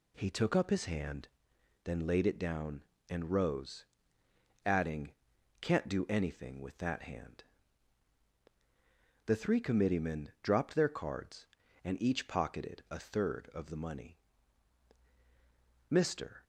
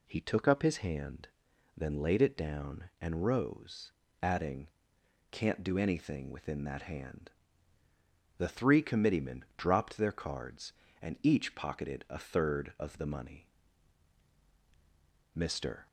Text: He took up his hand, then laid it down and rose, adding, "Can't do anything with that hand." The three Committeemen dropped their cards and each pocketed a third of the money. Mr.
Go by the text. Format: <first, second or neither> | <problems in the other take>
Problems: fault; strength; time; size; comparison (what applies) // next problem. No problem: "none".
first | says "within" for "with"; at 6.3 s